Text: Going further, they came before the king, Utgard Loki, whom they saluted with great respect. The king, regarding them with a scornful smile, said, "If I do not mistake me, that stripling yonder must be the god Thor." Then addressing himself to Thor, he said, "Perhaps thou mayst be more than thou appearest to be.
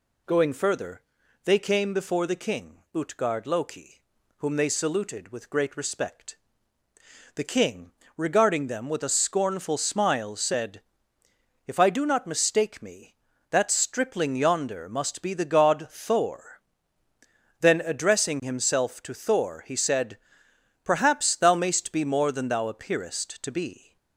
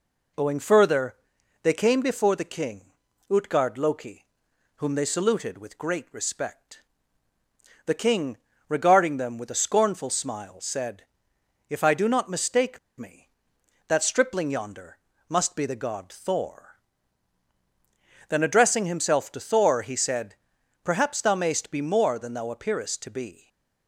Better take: first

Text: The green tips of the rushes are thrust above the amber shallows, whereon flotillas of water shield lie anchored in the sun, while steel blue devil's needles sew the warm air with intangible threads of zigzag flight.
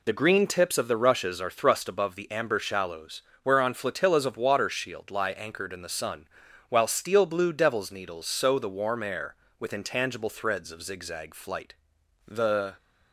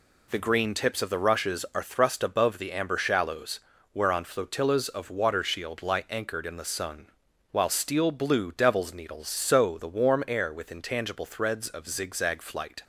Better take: second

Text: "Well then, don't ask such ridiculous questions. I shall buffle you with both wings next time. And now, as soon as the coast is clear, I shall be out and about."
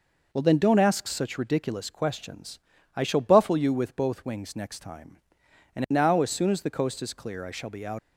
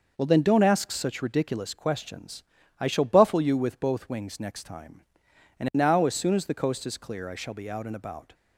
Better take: second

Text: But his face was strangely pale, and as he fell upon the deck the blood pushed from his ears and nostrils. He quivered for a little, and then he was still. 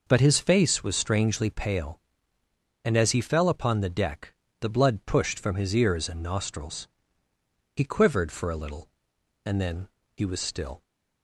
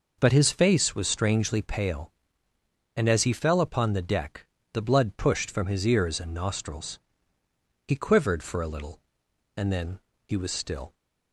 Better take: neither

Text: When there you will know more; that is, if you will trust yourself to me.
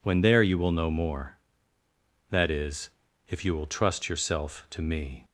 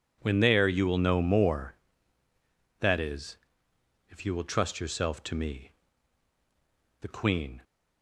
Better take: first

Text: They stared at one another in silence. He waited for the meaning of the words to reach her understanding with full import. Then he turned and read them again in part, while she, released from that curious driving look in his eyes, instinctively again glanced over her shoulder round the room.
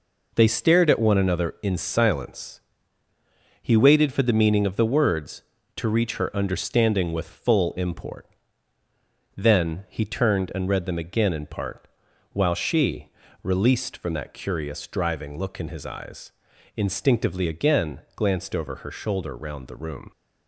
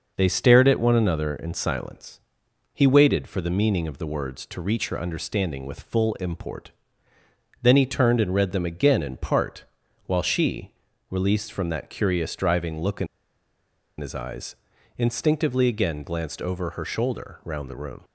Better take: first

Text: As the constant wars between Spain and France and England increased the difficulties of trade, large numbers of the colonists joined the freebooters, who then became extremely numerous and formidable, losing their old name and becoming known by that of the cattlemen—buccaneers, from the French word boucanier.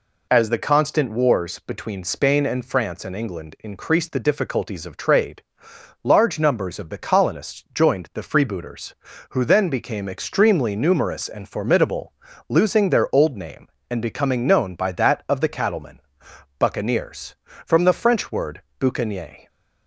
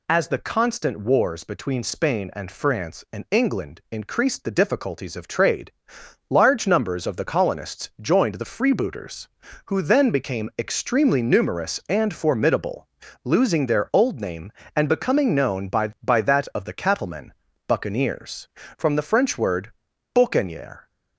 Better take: first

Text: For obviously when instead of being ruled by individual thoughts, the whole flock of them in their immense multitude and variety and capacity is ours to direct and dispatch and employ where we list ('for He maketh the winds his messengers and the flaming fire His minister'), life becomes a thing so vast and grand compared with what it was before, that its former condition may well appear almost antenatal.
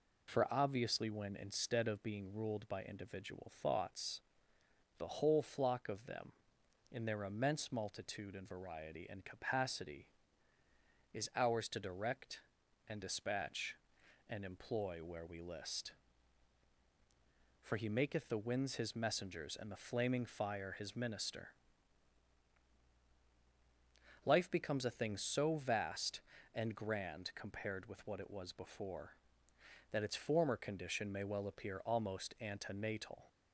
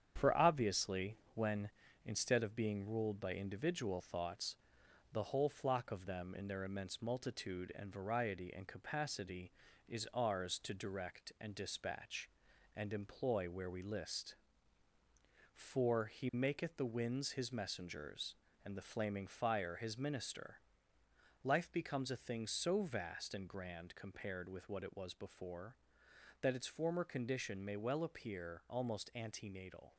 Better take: first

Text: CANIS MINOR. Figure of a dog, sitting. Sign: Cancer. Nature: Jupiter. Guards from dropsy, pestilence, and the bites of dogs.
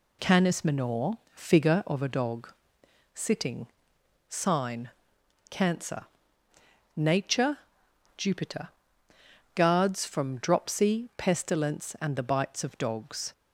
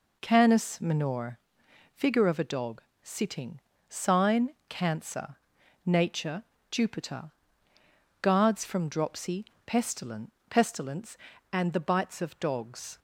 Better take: first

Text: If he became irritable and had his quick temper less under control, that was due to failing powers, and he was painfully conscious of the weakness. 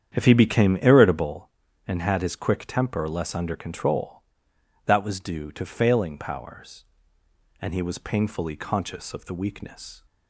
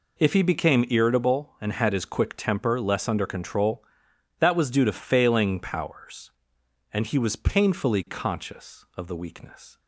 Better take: second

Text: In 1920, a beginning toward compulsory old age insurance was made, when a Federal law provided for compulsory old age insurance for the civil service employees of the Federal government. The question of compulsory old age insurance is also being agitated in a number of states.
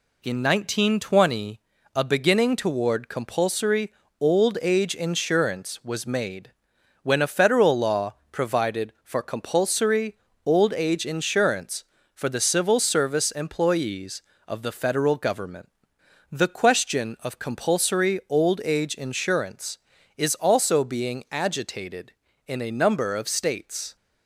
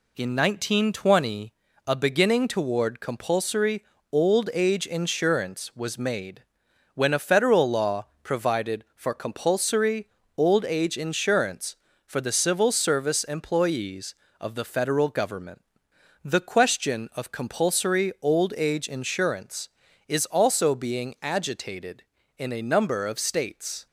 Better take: neither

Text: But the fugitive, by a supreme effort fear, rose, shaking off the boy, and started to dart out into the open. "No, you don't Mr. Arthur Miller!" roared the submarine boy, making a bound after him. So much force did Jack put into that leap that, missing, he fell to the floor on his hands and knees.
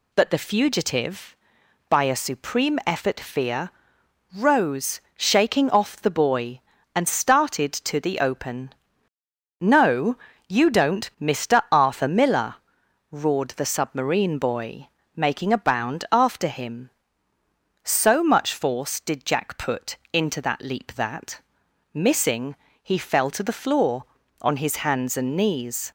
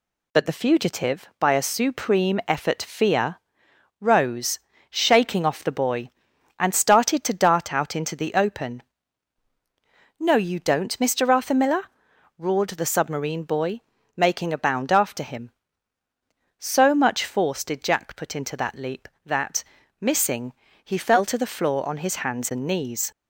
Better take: second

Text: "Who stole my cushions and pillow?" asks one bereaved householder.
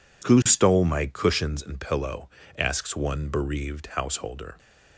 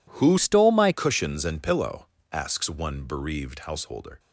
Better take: first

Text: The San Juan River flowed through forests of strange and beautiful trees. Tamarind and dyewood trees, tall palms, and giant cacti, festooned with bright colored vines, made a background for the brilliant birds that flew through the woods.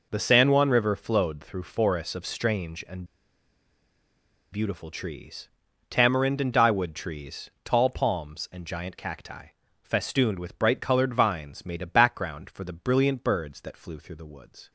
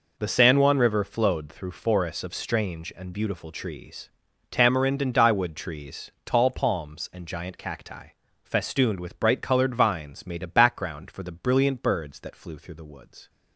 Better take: second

